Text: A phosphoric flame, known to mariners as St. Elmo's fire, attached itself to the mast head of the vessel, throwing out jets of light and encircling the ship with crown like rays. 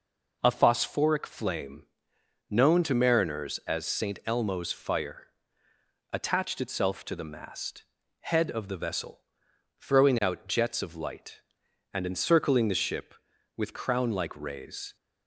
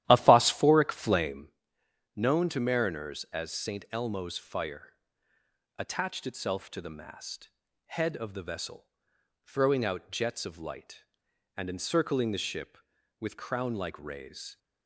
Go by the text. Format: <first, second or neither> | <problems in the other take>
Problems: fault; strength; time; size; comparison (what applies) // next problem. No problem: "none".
first | starts louder than the rest; strong; until 1.5 s; 13 dB // pauses between "mast" and "head"; at 7.4 s; 0.38 s long; also in the first